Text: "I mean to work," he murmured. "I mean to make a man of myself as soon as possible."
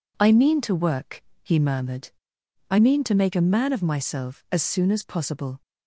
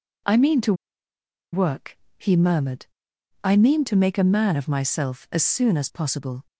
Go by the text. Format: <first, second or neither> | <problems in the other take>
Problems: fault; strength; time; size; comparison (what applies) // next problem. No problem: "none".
first | pauses between "to" and "work"; noticeable; at 0.7 s; 0.79 s long